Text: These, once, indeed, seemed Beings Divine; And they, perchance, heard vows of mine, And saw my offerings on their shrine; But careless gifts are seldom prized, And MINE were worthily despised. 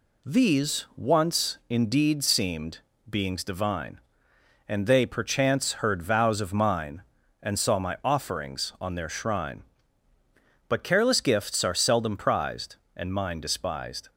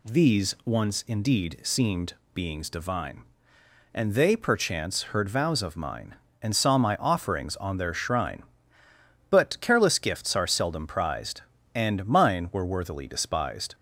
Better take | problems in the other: second | pauses between "seemed" and "Beings"; slight; at 2.7 s; 0.30 s long; slight in the second // skips "were worthily"; at 13.3 s

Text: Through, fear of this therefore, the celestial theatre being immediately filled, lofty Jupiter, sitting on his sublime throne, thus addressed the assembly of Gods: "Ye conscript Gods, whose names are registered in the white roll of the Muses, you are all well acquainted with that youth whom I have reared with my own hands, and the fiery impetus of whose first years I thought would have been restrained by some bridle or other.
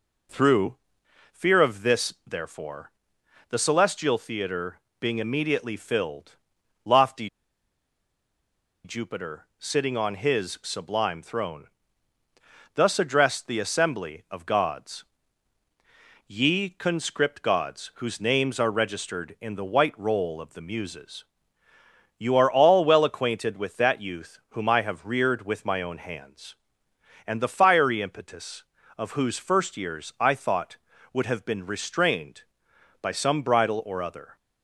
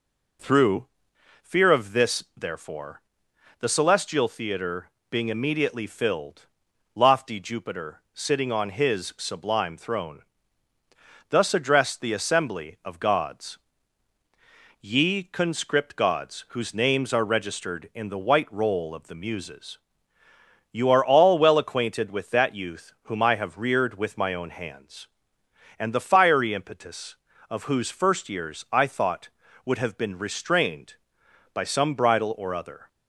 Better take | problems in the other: second | pauses between "theatre" and "being"; slight; at 4.7 s; 0.22 s long; slight in the second // pauses between "lofty" and "Jupiter"; strong; at 7.2 s; 1.5 s long

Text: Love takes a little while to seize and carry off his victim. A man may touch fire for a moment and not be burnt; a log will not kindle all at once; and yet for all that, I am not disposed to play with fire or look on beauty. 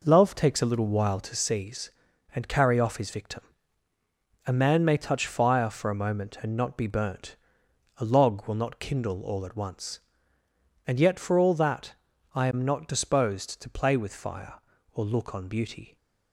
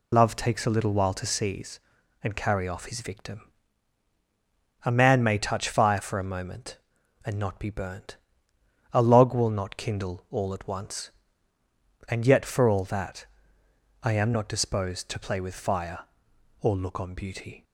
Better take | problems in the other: first | loses the start of "Love"; at 0.1 s; 70 ms

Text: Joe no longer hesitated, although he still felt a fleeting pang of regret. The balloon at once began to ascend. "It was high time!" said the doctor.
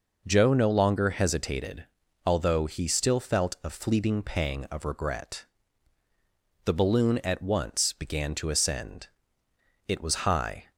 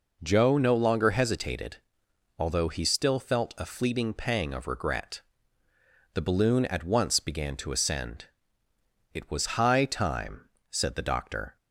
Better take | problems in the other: second | stops before "time said the doctor"; at 10.7 s

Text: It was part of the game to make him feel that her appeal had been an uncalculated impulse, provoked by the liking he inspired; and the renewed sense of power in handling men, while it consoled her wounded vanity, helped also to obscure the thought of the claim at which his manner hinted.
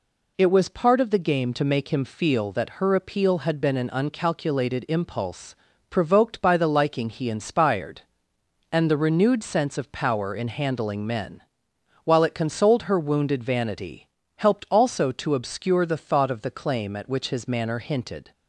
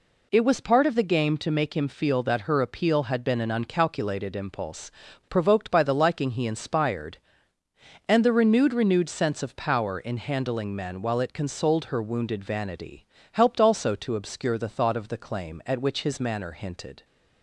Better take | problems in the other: first | says "renewed" twice; at 8.7 s

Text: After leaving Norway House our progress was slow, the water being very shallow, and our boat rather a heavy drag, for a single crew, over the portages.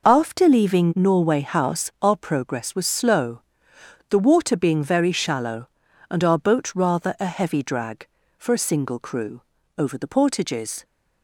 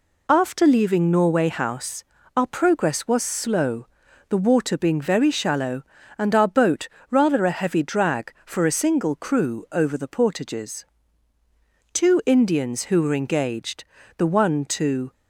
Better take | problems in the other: first | pauses between "House" and "our"; slight; at 2.0 s; 0.32 s long // pauses between "boat" and "rather"; slight; at 6.8 s; 0.24 s long // goes on to say "Two Indians who were engaged the one to"; strong; from 11.9 s on; 3.1 s long

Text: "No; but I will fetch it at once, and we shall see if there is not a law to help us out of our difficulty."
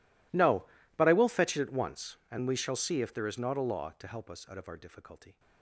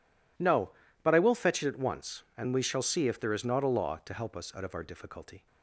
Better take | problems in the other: second | gets quieter; strong; throughout; 24.5 dB

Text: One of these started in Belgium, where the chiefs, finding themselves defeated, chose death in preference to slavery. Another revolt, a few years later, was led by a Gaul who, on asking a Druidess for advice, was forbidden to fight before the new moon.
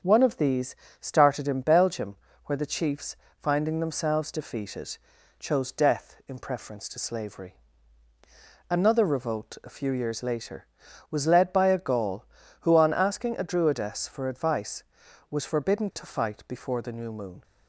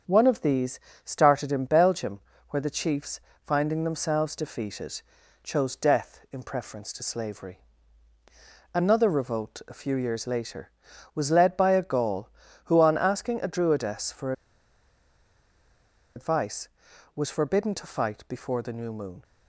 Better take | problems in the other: first | starts louder than the rest; strong; until 1.3 s; 7.5 dB; strong in the first // pauses between "these" and "started"; slight; at 0.7 s; 0.26 s long; slight in the first // pauses between "for" and "advice"; strong; at 14.3 s; 1.8 s long

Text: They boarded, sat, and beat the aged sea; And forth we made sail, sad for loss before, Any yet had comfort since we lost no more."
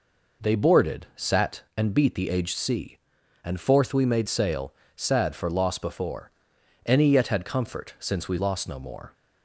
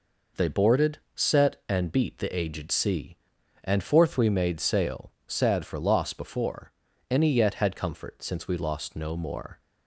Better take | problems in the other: first | says "set" for "sat"; at 1.1 s

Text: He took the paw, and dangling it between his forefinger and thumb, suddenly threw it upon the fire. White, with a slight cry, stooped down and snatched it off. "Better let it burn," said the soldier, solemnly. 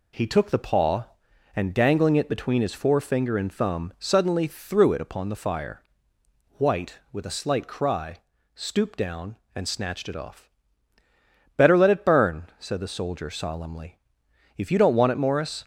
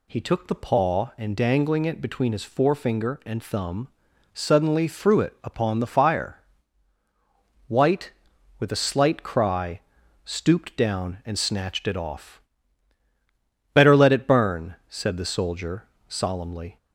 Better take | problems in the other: second | goes on to say "If you don't want it Morris"; noticeable; from 14.5 s on; 1.0 s long

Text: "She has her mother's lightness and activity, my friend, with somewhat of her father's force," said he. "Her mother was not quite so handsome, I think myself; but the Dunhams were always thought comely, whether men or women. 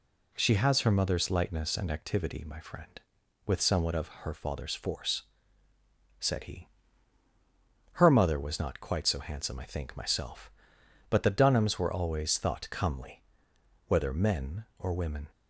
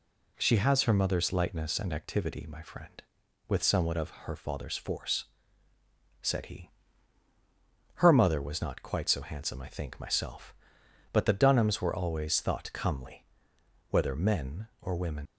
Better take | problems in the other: first | leaves "women" unfinished; at 15.2 s; 75 ms

